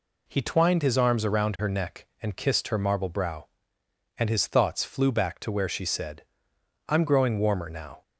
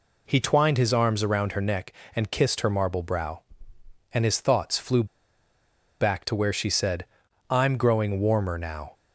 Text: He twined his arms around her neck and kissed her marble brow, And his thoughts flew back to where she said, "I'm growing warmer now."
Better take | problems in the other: first | pauses between "flew" and "back"; noticeable; at 5.0 s; 0.95 s long

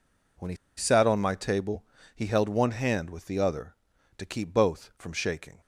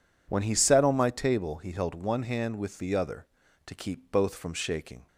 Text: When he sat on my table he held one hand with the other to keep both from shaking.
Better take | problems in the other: second | pauses between "he" and "sat"; slight; at 0.5 s; 0.21 s long // pauses between "table" and "he"; slight; at 1.8 s; 0.32 s long

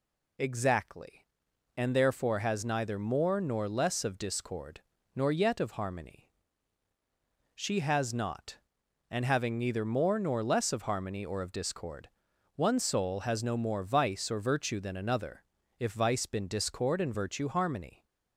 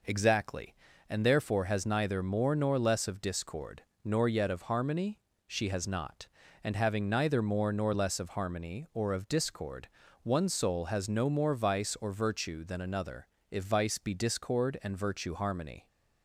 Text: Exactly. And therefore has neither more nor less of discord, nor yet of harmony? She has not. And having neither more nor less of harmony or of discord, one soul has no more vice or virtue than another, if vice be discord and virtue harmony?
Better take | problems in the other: second | says "been" for "be"; at 16.2 s

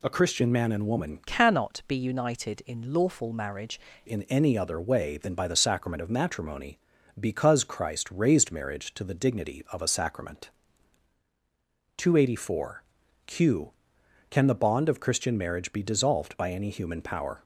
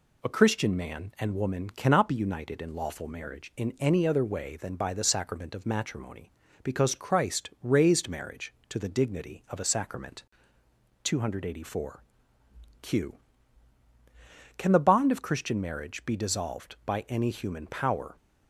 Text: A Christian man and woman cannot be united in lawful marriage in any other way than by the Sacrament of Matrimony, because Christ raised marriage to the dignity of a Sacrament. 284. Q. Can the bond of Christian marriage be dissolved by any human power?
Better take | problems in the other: second | changes voice from "cannot" to "marriage"; from 1.2 to 3.7 s; 2.5 s long

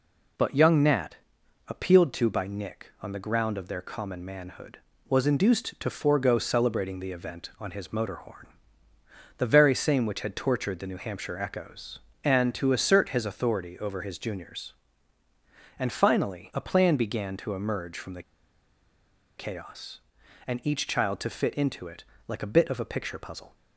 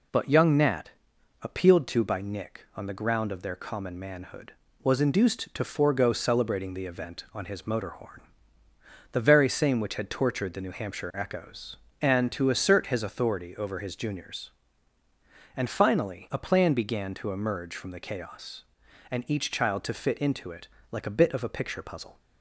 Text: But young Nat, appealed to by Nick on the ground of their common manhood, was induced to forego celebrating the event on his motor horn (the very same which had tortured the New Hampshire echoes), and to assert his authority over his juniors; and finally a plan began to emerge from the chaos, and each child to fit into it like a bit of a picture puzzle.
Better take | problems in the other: second | pauses between "the" and "chaos"; at 18.2 s; 1.1 s long // pauses between "it" and "like"; slight; at 22.0 s; 0.24 s long; slight in the second

